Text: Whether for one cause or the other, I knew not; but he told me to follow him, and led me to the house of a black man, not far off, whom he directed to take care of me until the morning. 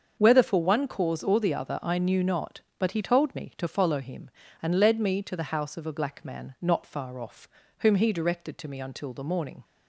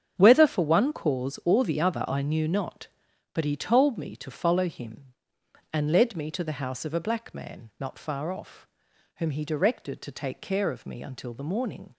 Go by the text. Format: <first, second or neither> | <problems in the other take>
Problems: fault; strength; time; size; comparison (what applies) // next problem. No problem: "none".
second | starts louder than the rest; until 1.2 s; 6.5 dB; strong in the second // skips "take care of"; at 8.6 s